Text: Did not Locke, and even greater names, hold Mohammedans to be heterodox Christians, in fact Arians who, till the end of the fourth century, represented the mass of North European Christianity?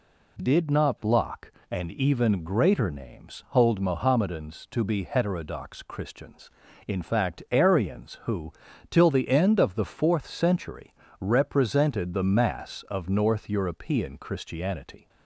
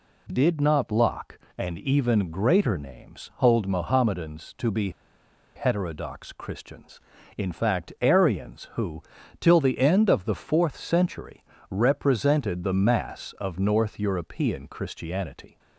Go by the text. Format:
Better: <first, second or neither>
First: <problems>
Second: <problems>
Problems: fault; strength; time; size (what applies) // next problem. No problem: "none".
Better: first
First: none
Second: pauses between "be" and "heterodox"; noticeable; at 4.8 s; 0.65 s long